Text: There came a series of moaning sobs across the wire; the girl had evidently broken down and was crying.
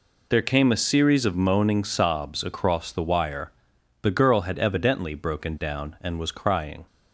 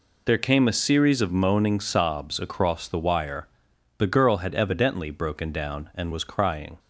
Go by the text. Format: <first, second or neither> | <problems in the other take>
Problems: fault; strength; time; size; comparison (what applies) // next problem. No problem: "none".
neither | none